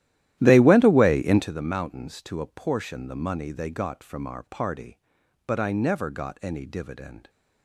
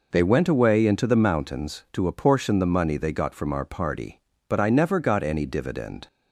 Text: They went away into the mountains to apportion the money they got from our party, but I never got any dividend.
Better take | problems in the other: second | starts louder than the rest; strong; until 1.5 s; 13 dB

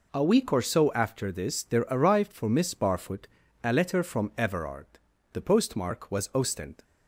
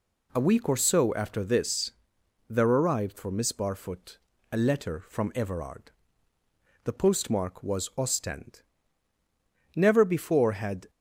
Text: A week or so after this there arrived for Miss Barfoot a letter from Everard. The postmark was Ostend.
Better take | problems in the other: first | pauses between "this" and "there"; noticeable; at 1.8 s; 0.58 s long // pauses between "Barfoot" and "a"; slight; at 4.1 s; 0.34 s long; slight in the first // goes on to say "Never before had"; noticeable; from 9.7 s on; 1.1 s long

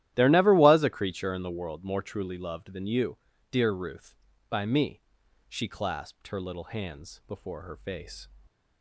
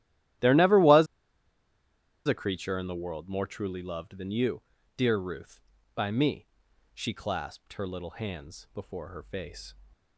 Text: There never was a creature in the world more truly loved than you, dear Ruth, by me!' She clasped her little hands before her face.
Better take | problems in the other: first | starts louder than the rest; strong; until 2.6 s; 13 dB; strong in the first // pauses between "was" and "a"; at 1.0 s; 1.2 s long

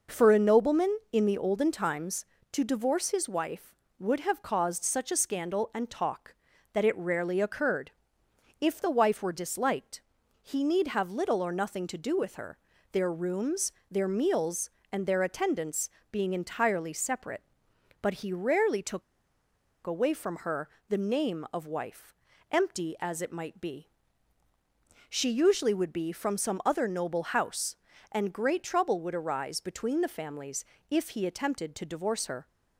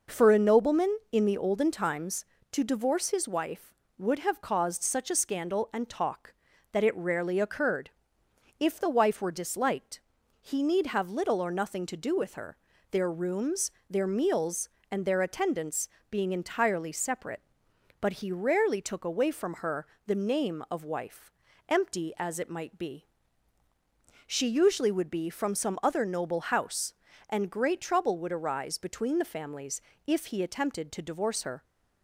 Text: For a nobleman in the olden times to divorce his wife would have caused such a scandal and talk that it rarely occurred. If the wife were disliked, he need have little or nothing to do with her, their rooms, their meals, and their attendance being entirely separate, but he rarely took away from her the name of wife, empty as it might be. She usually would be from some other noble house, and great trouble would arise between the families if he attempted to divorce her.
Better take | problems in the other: second | pauses between "attendance" and "being"; slight; at 15.8 s; 0.20 s long; slight in the second // pauses between "took" and "away"; noticeable; at 19.0 s; 0.84 s long // pauses between "her" and "the"; slight; at 20.6 s; 0.22 s long; slight in the second // pauses between "families" and "if"; slight; at 30.6 s; 0.24 s long; slight in the second

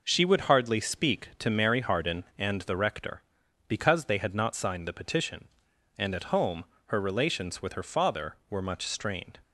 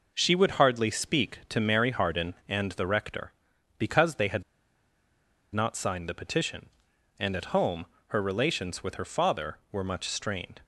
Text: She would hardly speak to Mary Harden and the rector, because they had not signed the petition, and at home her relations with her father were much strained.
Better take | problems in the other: first | pauses between "had" and "not"; at 4.4 s; 1.1 s long // pauses between "home" and "her"; slight; at 7.8 s; 0.24 s long; slight in the first

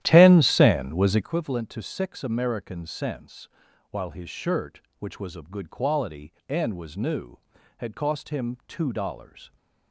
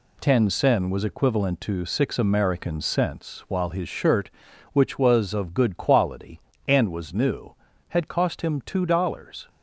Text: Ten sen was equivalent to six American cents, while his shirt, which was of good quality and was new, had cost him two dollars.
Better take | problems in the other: second | starts louder than the rest; strong; until 1.3 s; 12.5 dB

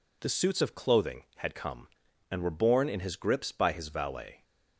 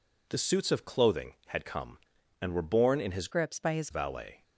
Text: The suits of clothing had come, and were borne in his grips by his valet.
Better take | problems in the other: first | changes voice from "grips" to "his"; from 3.3 to 3.9 s; 0.6 s long

